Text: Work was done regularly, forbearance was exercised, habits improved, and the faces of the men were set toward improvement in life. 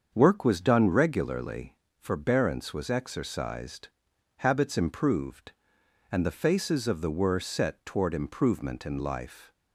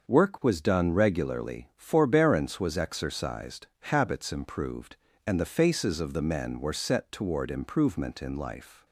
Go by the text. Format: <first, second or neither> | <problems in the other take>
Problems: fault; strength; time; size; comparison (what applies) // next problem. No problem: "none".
second | starts louder than the rest; until 1.1 s; 7 dB; also in the second // skips "men"; at 7.1 s